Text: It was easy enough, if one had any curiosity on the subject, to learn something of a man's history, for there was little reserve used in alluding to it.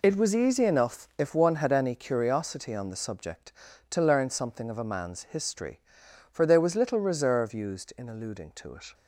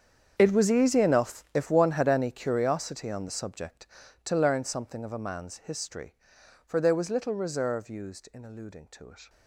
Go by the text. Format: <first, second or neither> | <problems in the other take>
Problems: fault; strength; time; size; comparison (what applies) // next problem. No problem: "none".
first | gets quieter; strong; throughout; 17.5 dB